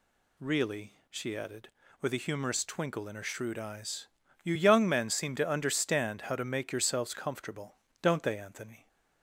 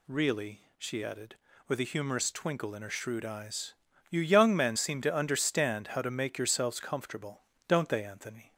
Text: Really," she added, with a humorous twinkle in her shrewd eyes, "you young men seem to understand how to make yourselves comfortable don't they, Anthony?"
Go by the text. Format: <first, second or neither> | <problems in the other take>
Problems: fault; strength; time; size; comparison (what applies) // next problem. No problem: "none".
neither | pauses between "comfortable" and "don't"; slight; the same in both